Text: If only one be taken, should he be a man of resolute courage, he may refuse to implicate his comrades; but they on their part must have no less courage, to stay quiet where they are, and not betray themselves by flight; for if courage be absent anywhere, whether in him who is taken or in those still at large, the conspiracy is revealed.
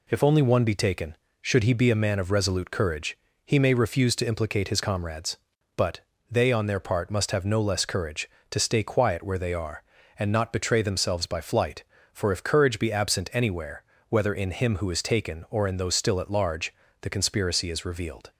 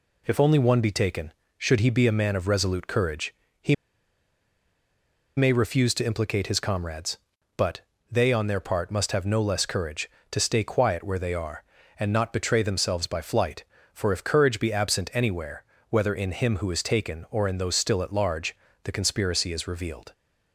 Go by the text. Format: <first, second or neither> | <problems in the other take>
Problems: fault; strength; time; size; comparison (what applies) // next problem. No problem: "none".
first | pauses between "he" and "may"; strong; at 3.7 s; 1.6 s long // pauses between "but" and "they"; slight; at 7.7 s; 0.32 s long; slight in the first